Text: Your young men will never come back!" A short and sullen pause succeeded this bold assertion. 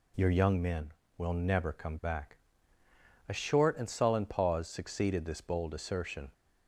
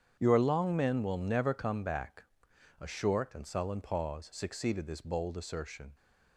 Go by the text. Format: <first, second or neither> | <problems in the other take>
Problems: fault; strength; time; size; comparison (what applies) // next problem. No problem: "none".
first | starts louder than the rest; strong; until 1.2 s; 8.5 dB // says "long" for "young"; at 0.3 s